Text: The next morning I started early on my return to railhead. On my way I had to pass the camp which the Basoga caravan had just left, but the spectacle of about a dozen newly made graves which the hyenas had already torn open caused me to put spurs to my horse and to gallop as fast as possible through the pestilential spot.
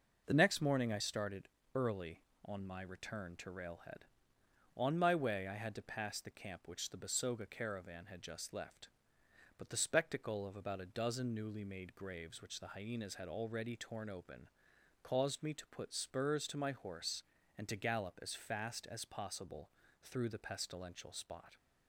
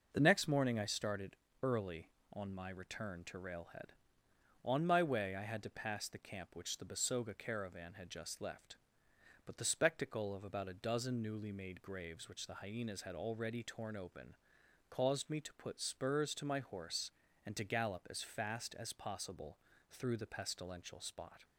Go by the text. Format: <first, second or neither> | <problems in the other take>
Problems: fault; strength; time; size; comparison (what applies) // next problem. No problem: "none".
neither | pauses between "started" and "early"; slight; the same in both // pauses between "open" and "caused"; noticeable; the same in both // pauses between "possible" and "through"; slight; the same in both